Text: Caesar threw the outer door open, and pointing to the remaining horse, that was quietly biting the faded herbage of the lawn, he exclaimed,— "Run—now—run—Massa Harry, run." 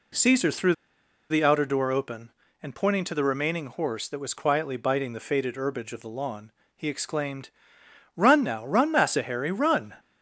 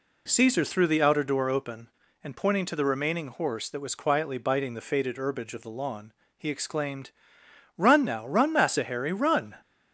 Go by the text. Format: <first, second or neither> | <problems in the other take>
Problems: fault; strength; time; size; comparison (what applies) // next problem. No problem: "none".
second | pauses between "threw" and "the"; noticeable; at 0.7 s; 0.55 s long